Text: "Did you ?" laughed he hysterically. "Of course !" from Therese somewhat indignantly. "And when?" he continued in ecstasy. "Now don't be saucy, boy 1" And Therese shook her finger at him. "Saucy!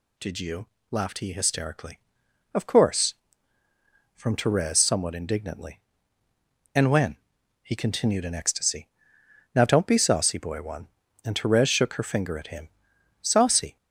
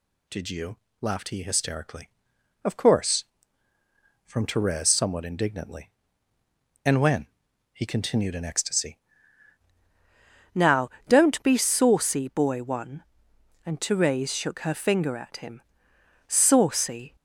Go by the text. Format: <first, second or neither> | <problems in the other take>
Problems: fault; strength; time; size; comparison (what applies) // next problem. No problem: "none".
first | changes voice at "Now"; from 10.5 s on; 6.6 s long // pauses between "Now" and "don't"; slight; at 10.8 s; 0.18 s long